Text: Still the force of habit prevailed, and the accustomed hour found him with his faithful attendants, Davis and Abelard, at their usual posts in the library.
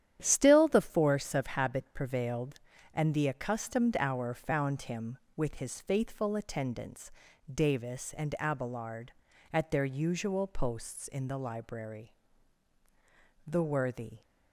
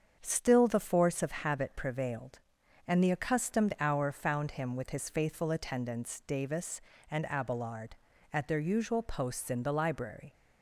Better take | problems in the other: second | starts louder than the rest; strong; until 1.2 s; 10.5 dB; also in the second // goes on to say "The worthy"; noticeable; from 13.4 s on; 0.74 s long

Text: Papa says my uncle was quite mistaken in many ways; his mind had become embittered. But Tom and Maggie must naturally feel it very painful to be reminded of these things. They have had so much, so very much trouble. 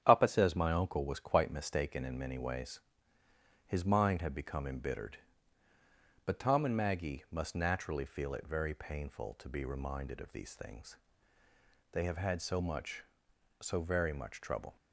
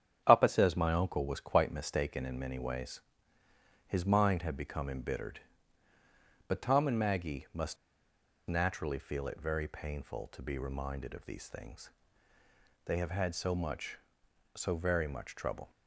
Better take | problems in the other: first | starts louder than the rest; strong; until 1.2 s; 8.5 dB; strong in the first // pauses between "must" and "naturally"; noticeable; at 7.7 s; 0.71 s long

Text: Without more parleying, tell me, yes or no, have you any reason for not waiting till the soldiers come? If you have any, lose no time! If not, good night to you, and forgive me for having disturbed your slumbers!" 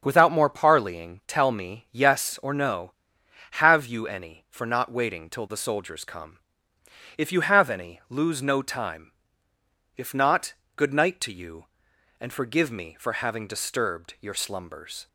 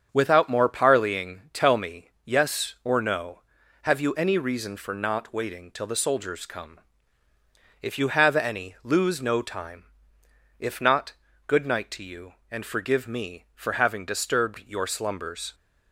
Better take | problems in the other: second | starts louder than the rest; strong; until 1.0 s; 7 dB; strong in the second // skips "reason"; at 4.4 s

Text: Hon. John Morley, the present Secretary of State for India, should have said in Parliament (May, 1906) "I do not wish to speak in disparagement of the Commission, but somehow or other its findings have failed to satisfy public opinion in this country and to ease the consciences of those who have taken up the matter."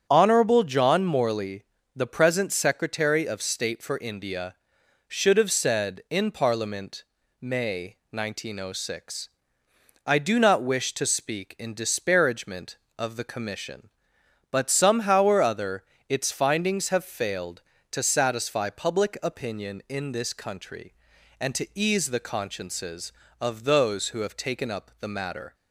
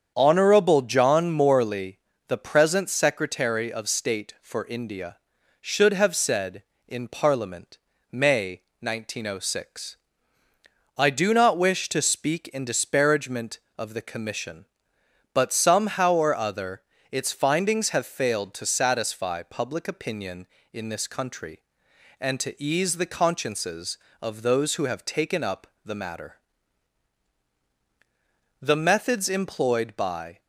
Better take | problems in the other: first | starts louder than the rest; strong; until 1.1 s; 7.5 dB; strong in the first // pauses between "other" and "its"; slight; at 16.8 s; 0.30 s long; slight in the first // pauses between "up" and "the"; slight; at 25.6 s; 0.18 s long // goes on to say "The methods employed by"; strong; from 28.6 s on; 1.7 s long

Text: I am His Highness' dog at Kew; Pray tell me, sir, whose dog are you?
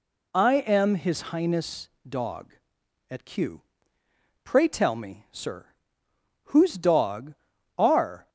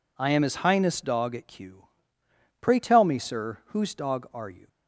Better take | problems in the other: second | pauses between "Highness" and "dog"; slight; at 1.8 s; 0.20 s long // stops before "you"; at 8.2 s

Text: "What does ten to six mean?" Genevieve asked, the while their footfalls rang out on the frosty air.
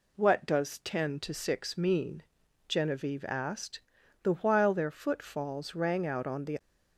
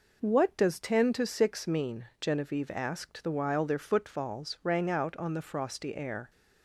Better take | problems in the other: second | stops before "frosty air"; at 6.5 s

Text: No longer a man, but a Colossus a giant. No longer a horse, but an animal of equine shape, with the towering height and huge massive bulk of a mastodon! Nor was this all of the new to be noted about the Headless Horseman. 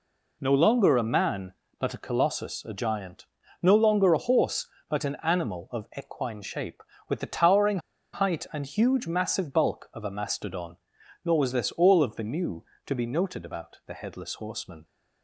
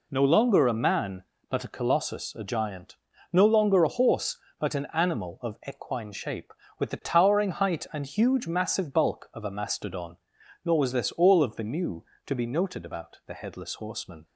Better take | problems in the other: second | pauses between "towering" and "height"; slight; at 7.7 s; 0.35 s long

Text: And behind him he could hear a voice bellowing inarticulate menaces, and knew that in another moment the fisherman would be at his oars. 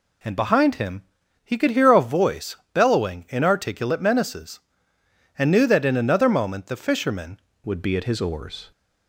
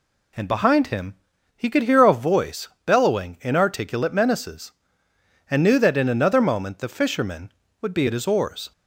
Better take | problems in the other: second | pauses between "him" and "he"; at 1.0 s; 0.40 s long; also in the second // pauses between "voice" and "bellowing"; slight; at 2.5 s; 0.18 s long; slight in the second // changes voice at "would"; from 7.6 s on; 1.1 s long

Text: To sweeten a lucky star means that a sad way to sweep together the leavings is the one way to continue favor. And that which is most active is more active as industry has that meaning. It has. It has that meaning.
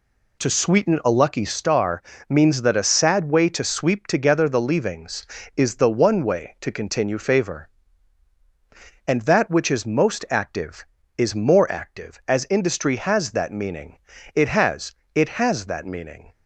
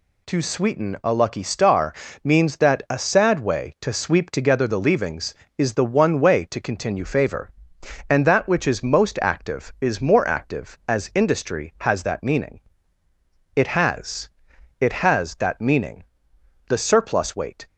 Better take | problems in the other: first | pauses between "star" and "means"; slight; at 1.9 s; 0.30 s long; slight in the first // goes on to say "The surplus weight"; noticeable; from 16.6 s on; 0.98 s long

